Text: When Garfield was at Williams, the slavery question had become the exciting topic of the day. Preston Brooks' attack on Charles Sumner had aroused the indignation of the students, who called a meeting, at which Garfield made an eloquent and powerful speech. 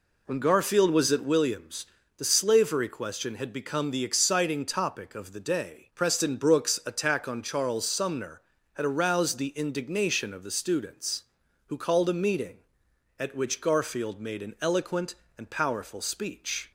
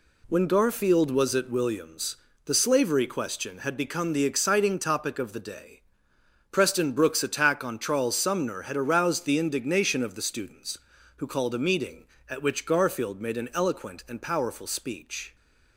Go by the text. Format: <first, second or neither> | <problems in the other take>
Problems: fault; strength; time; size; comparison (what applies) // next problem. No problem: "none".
second | starts louder than the rest; slight; until 1.4 s; 3.5 dB